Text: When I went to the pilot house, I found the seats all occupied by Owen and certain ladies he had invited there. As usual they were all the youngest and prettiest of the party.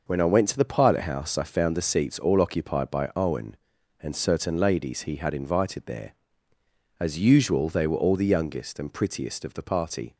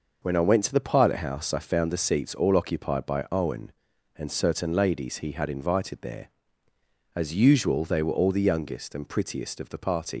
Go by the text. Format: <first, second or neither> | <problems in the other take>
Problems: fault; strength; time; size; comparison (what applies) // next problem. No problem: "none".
first | leaves "party" unfinished; at 10.1 s; 110 ms